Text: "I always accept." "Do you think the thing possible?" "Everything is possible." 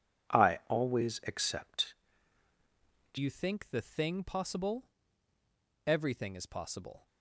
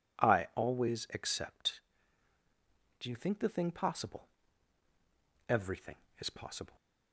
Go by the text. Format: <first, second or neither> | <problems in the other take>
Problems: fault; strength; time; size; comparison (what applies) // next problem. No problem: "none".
second | changes voice at "you"; from 3.1 s on; 3.9 s long